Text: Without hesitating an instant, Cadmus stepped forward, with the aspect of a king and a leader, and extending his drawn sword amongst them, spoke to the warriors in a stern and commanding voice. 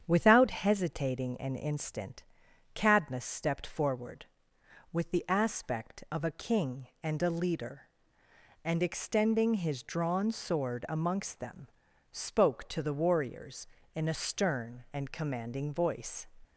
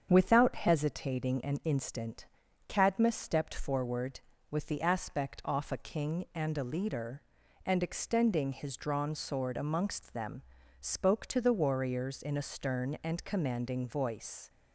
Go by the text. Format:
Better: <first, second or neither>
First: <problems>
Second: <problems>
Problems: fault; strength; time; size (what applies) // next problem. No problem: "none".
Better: first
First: starts louder than the rest; strong; until 1.0 s; 8 dB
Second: starts louder than the rest; strong; until 1.1 s; 7.5 dB // says "off" for "of"; at 5.4 s